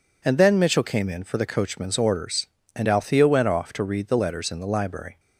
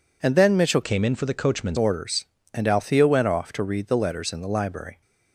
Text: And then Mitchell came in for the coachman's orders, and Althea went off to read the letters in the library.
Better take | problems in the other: first | changes voice from "came" to "coachman's"; from 0.8 to 1.7 s; 0.9 s long

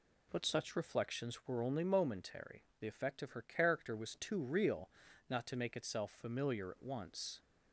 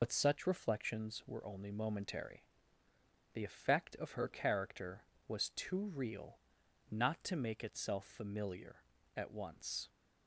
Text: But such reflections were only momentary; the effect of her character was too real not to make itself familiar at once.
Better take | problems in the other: first | loses the start of "But"; at 0.0 s; 55 ms // pauses between "real" and "not"; noticeable; at 6.3 s; 0.52 s long; also in the first

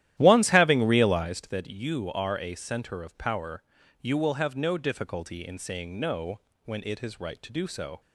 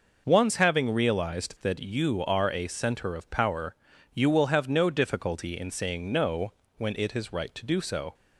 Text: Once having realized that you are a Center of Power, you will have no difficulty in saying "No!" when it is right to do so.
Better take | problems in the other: second | starts louder than the rest; strong; until 1.3 s; 12.5 dB

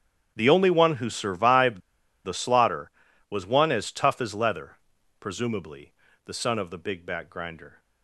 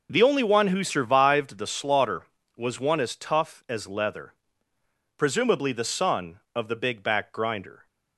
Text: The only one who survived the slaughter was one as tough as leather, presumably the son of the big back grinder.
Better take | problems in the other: second | starts louder than the rest; strong; until 1.3 s; 9 dB // pauses between "survived" and "the"; at 1.8 s; 0.44 s long // pauses between "presumably" and "the"; slight; at 5.9 s; 0.32 s long

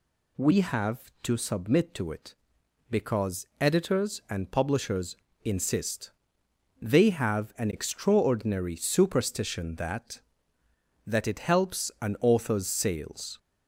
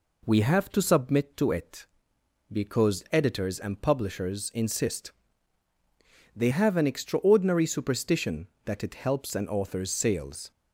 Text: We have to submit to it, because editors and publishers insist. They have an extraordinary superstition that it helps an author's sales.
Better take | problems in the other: second | pauses between "because" and "editors"; slight; at 3.4 s; 0.16 s long // pauses between "publishers" and "insist"; slight; at 5.1 s; 0.30 s long // says "that" twice; at 11.0 s

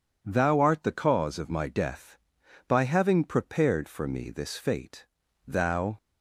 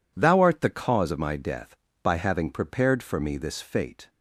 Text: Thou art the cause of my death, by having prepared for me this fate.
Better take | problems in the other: second | goes on to say "Thou"; from 5.4 s on; 0.50 s long

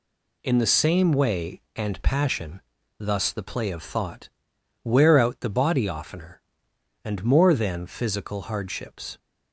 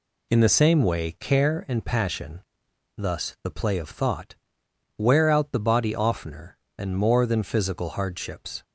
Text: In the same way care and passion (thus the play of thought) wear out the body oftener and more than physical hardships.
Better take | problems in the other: second | skips "care"; at 1.6 s

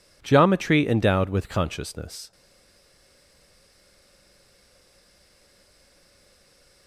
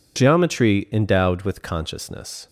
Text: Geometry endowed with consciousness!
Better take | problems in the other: second | stays silent after the last word; strong; from 2.3 s on; 4.5 s long

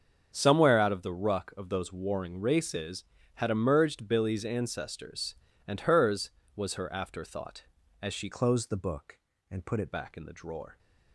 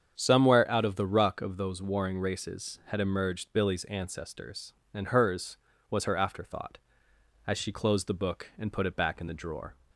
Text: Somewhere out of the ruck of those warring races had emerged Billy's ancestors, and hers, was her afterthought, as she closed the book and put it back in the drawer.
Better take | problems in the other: second | starts louder than the rest; until 1.3 s; 7 dB; strong in the second // changes voice from "closed" to "it"; from 8.3 to 9.9 s; 1.6 s long

